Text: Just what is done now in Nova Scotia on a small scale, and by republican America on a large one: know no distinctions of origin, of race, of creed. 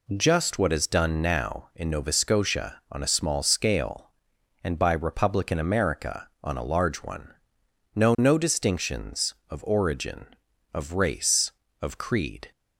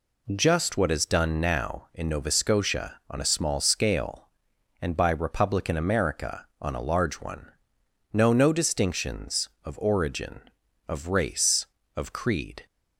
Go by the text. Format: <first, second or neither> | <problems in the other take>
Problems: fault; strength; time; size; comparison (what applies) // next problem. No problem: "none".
neither | none